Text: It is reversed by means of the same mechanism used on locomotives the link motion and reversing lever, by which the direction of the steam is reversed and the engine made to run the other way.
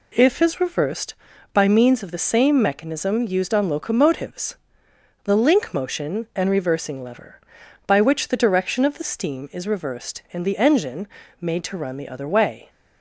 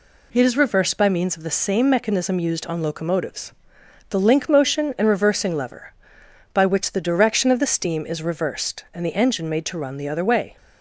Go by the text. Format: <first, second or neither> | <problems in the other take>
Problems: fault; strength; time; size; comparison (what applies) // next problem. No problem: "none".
second | says "If" for "It"; at 0.1 s // pauses between "locomotives" and "the"; noticeable; at 4.5 s; 0.66 s long; noticeable in the second // pauses between "engine" and "made"; slight; at 11.0 s; 0.34 s long